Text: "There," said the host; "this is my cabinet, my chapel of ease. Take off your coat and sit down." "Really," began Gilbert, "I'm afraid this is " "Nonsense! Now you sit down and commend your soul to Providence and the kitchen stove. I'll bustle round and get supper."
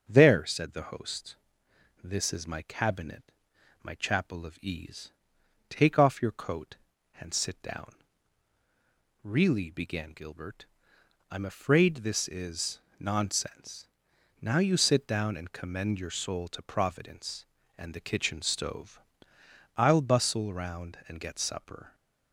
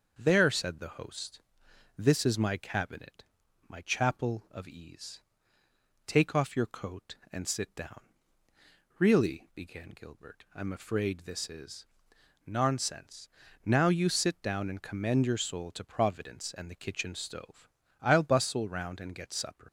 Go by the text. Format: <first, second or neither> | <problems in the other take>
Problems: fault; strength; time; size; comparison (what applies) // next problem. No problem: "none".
first | starts louder than the rest; until 1.1 s; 6.5 dB; also in the first // leaves "supper" unfinished; at 19.6 s; 75 ms